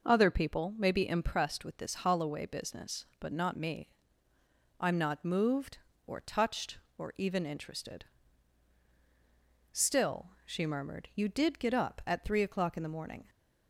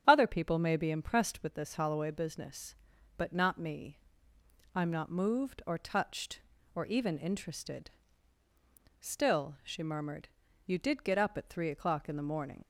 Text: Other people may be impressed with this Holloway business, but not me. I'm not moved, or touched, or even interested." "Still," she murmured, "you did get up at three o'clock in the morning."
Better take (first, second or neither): first